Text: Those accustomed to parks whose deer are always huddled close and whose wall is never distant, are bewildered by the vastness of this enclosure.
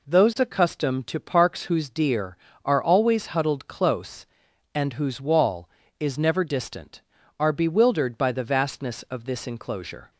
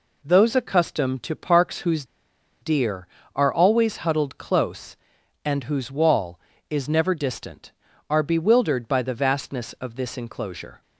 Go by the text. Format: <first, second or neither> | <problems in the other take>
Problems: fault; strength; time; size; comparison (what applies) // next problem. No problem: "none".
first | pauses between "whose" and "deer"; noticeable; at 2.0 s; 0.57 s long